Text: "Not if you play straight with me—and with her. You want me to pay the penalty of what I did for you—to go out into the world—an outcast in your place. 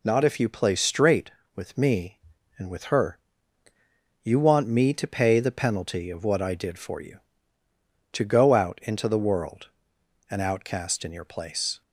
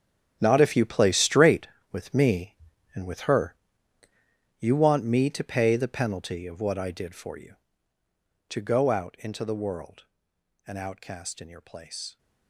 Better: first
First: none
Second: gets quieter; strong; throughout; 14.5 dB

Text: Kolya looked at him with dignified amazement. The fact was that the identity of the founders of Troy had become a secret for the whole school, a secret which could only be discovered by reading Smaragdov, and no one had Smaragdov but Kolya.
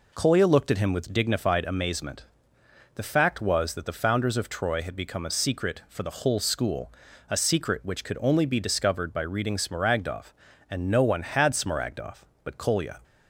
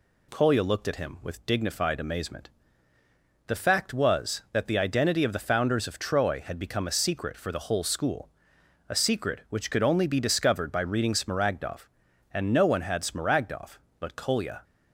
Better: second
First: skips "the identity of"; at 3.8 s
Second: none

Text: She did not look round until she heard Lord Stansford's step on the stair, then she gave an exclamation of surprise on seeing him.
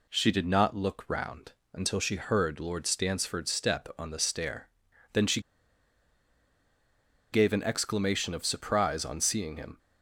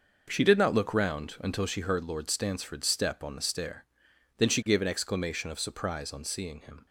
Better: second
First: pauses between "round" and "until"; slight; at 1.5 s; 0.20 s long // pauses between "she" and "gave"; strong; at 5.3 s; 1.9 s long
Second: none

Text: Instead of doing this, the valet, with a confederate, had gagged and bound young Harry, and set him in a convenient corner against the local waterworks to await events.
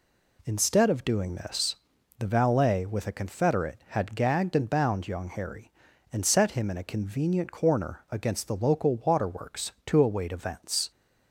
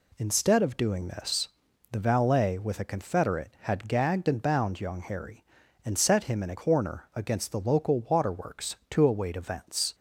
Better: first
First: none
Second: skips "convenient"; at 6.5 s

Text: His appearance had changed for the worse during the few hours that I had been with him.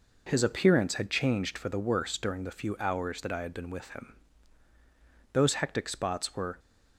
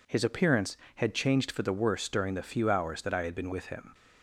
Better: second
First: goes on to say "Those hectic spots were"; noticeable; from 5.3 s on; 1.2 s long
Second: none

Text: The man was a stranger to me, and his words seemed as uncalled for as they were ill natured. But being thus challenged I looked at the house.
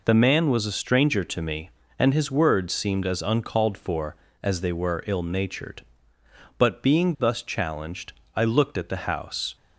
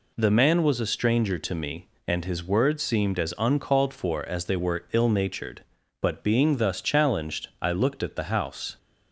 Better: neither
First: pauses between "challenged" and "I"; slight; at 8.1 s; 0.20 s long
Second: pauses between "challenged" and "I"; slight; at 7.4 s; 0.16 s long

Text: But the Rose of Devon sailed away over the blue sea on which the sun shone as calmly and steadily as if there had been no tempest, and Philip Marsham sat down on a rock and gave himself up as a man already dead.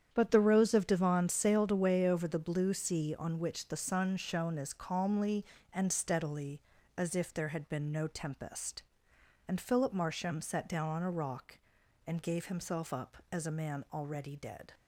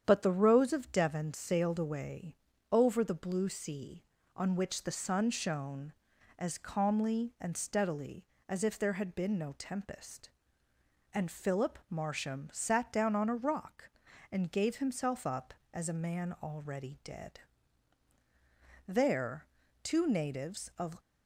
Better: first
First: starts louder than the rest; strong; until 1.1 s; 8.5 dB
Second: starts louder than the rest; strong; until 1.0 s; 8.5 dB // pauses between "away" and "over"; slight; at 2.3 s; 0.36 s long // goes on to say "There two natives of"; strong; from 18.8 s on; 2.1 s long

